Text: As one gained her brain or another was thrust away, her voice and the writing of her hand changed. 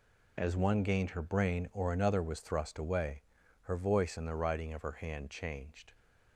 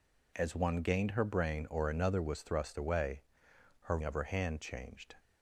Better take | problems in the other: first | skips "voice and the writing"; at 4.0 s

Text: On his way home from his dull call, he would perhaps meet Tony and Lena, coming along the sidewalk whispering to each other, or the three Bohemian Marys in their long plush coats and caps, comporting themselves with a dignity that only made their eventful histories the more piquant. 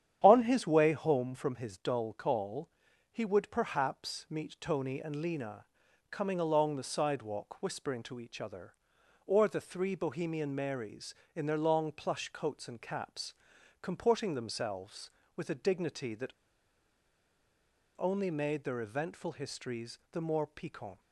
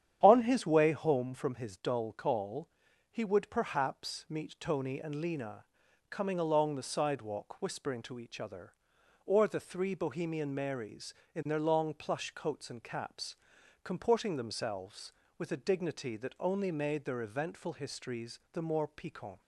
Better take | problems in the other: second | starts louder than the rest; strong; until 1.2 s; 9.5 dB; strong in the second // pauses between "that" and "only"; strong; at 16.3 s; 1.6 s long

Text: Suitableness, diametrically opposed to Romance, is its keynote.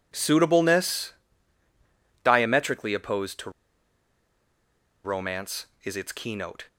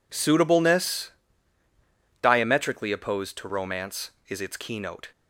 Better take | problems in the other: second | pauses between "to" and "Romance"; strong; at 3.4 s; 1.5 s long

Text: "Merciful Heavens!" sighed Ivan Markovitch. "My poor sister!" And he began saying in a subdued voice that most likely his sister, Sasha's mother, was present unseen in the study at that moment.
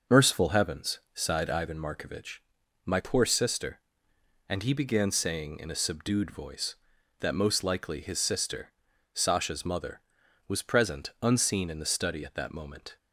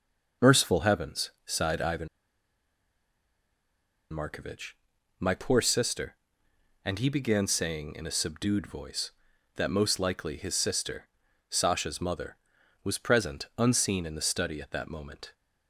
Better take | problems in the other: first | starts louder than the rest; until 1.5 s; 6.5 dB; also in the first // pauses between "Ivan" and "Markovitch"; strong; at 2.0 s; 2.0 s long

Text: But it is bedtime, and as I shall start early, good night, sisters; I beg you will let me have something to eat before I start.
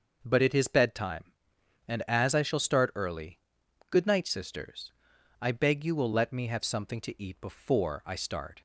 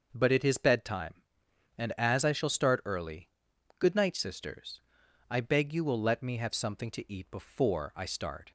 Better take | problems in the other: neither | none

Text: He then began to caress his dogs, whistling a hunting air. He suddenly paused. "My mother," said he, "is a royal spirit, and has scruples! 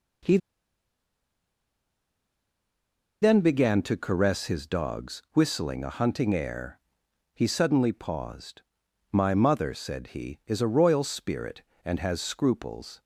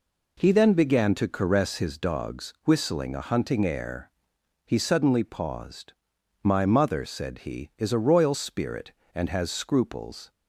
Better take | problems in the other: second | pauses between "He" and "then"; strong; at 0.3 s; 2.8 s long

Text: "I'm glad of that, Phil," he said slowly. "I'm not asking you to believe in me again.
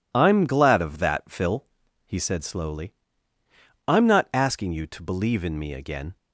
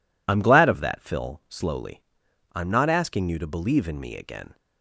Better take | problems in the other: first | skips "he said"; at 1.4 s

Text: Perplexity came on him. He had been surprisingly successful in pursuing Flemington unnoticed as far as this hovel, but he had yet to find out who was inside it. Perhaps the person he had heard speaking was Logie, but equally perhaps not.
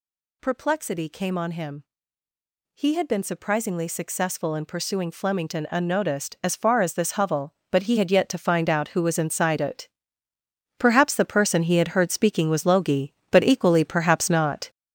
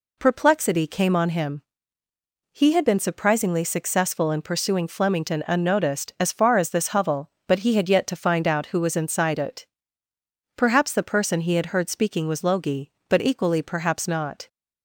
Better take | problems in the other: second | gets louder; strong; throughout; 7 dB

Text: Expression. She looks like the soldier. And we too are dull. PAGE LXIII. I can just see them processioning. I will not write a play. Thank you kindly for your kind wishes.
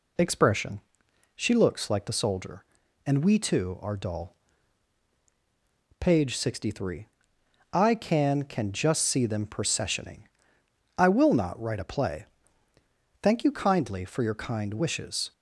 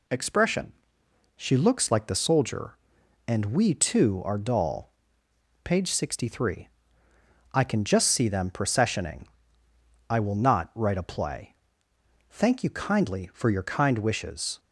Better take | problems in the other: second | says "can" twice; at 8.4 s

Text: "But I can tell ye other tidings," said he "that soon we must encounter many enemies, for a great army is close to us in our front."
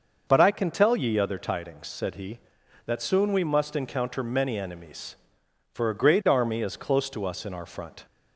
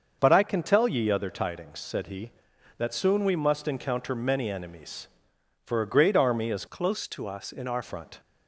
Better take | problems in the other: first | starts louder than the rest; until 1.2 s; 6.5 dB; also in the first // changes voice from "close" to "our"; from 6.6 to 7.8 s; 1.2 s long

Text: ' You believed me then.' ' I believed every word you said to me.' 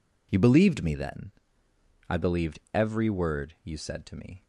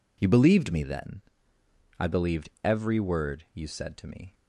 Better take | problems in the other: neither | none

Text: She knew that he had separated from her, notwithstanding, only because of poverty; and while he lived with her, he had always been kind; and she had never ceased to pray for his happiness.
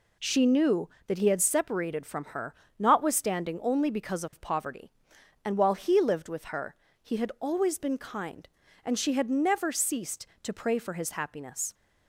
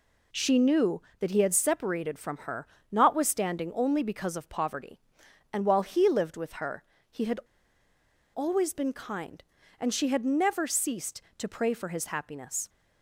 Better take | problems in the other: first | pauses between "had" and "always"; noticeable; at 7.3 s; 0.96 s long

